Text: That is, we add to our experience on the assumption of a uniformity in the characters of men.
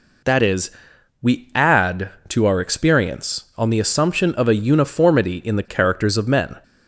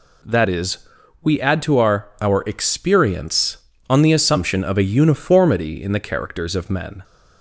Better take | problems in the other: first | says "our" twice; at 2.2 s

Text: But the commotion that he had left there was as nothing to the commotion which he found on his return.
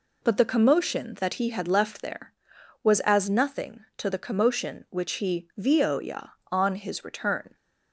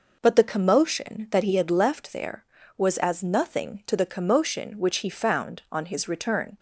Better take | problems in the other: second | says "vioya" for "found"; at 5.5 s

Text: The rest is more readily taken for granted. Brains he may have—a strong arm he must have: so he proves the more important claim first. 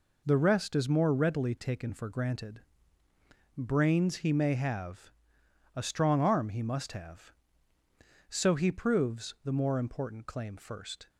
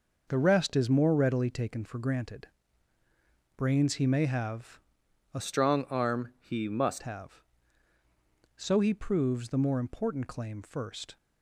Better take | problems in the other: first | changes voice from "strong" to "must"; from 5.4 to 7.0 s; 1.6 s long

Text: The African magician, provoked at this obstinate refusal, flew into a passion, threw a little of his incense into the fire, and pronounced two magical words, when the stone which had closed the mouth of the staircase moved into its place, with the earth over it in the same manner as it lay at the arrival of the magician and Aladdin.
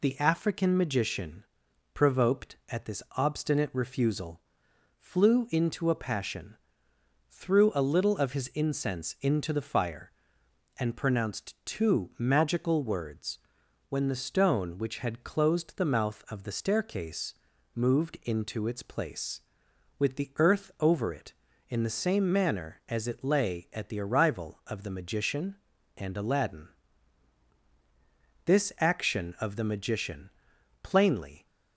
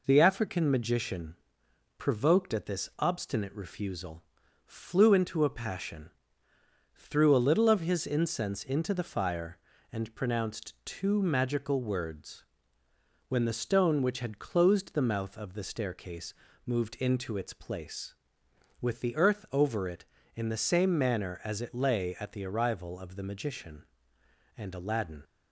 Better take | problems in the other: second | pauses between "staircase" and "moved"; at 17.3 s; 0.42 s long; slight in the second // goes on to say "This action of the magician plainly"; strong; from 28.4 s on; 3.0 s long

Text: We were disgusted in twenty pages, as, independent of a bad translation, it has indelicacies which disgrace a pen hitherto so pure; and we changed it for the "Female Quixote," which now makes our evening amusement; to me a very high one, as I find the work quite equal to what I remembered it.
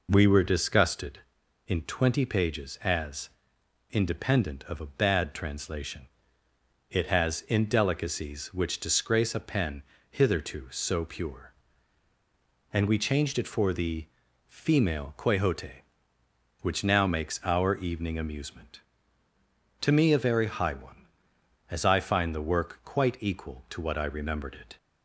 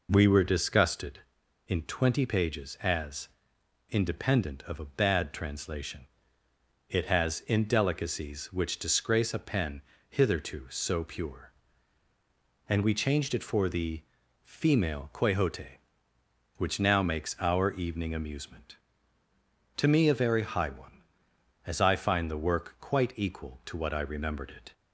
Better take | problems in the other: neither | pauses between "pen" and "hitherto"; slight; the same in both // pauses between "the" and "Female"; the same in both

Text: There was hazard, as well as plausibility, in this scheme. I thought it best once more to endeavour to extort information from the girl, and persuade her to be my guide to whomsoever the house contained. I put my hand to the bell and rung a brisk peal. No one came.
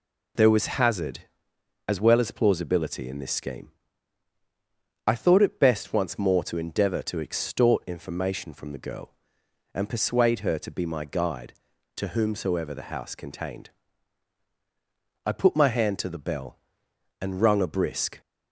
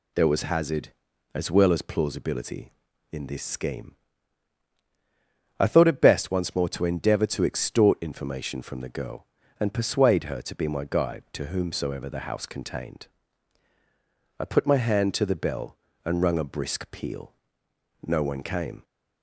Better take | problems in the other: second | stops before "peal No one came"; at 18.2 s

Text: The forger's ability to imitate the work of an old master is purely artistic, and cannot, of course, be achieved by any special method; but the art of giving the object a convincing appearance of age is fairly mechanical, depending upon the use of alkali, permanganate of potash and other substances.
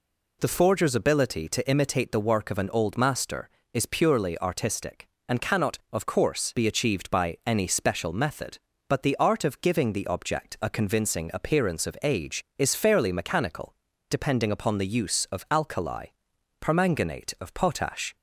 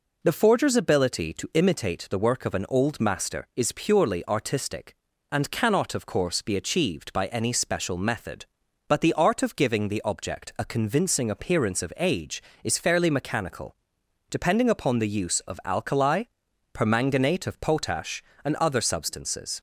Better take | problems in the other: second | stops before "and other substances"; at 18.1 s

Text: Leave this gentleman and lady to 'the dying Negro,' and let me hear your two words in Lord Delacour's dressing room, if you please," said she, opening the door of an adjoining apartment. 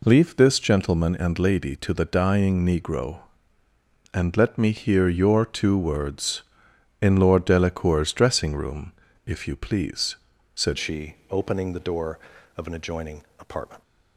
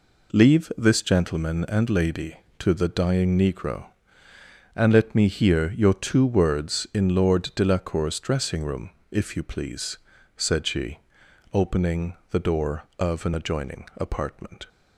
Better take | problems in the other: second | changes voice at "she"; from 10.7 s on; 3.1 s long // pauses between "adjoining" and "apartment"; slight; at 13.2 s; 0.16 s long

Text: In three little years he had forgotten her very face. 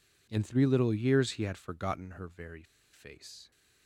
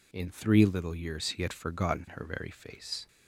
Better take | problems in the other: second | pauses between "very" and "face"; slight; at 2.6 s; 0.29 s long

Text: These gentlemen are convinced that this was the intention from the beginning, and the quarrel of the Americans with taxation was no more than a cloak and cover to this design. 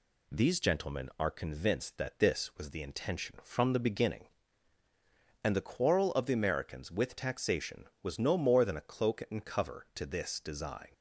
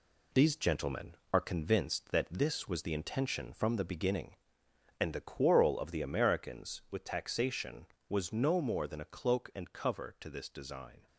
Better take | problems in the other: first | gets quieter; noticeable; throughout; 6 dB

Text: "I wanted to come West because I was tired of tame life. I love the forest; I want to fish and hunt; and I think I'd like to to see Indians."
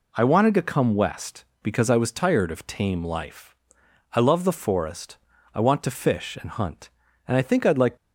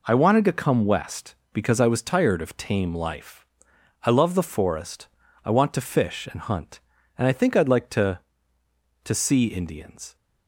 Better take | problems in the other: second | stops before "to to see Indians"; at 7.9 s

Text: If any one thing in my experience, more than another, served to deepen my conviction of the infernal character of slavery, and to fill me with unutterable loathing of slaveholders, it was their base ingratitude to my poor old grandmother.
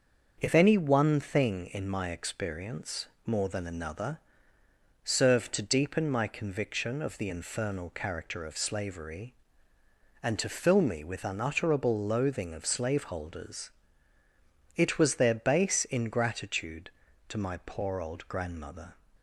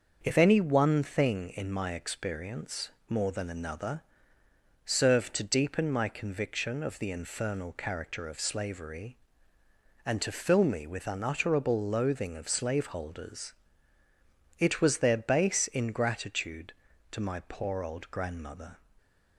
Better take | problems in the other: neither | starts louder than the rest; the same in both

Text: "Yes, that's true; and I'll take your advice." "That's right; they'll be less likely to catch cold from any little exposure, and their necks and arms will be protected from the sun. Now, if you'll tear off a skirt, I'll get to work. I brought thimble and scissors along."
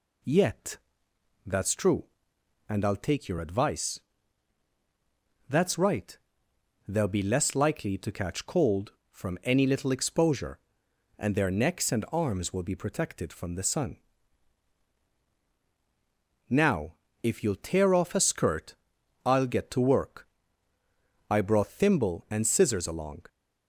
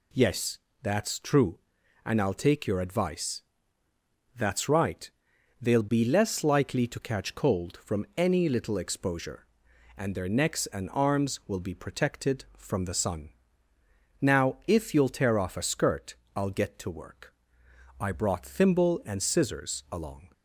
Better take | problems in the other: second | says "Yet" for "Yes"; at 0.2 s

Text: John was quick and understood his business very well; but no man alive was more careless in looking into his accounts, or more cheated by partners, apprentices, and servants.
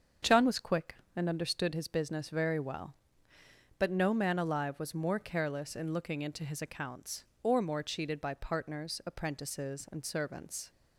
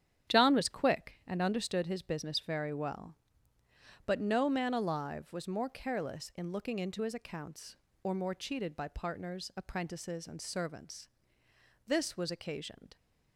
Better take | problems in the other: first | starts louder than the rest; strong; until 1.3 s; 9 dB; strong in the first // goes on to say "This was occasioned"; noticeable; from 11.8 s on; 1.1 s long

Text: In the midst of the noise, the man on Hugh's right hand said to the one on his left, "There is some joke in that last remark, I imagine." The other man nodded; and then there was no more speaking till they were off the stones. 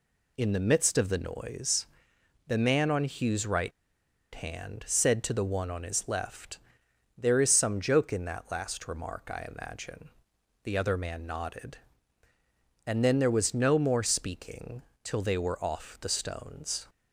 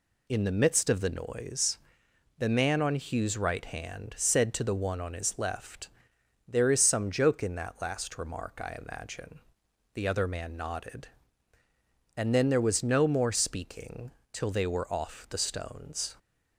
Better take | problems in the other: second | pauses between "right" and "hand"; noticeable; at 3.7 s; 0.62 s long // pauses between "speaking" and "till"; slight; at 14.8 s; 0.20 s long; slight in the second

